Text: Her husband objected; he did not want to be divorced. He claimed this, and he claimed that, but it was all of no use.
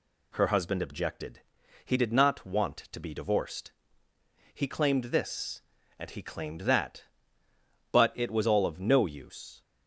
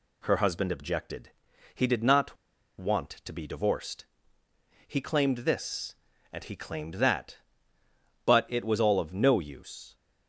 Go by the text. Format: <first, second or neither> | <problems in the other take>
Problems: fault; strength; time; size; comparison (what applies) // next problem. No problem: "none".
first | pauses between "not" and "want"; at 2.3 s; 0.43 s long